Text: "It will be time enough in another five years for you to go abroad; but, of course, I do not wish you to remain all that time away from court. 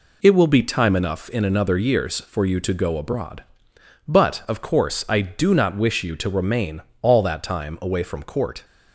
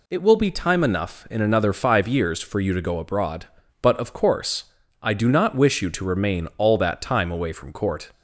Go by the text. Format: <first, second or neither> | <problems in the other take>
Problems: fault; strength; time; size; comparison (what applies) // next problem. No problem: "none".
second | skips "five"; at 1.7 s // pauses between "remain" and "all"; slight; at 6.8 s; 0.18 s long